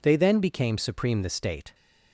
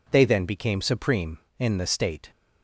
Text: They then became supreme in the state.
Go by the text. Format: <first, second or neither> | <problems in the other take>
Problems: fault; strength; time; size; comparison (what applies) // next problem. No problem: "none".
second | skips "in"; at 1.2 s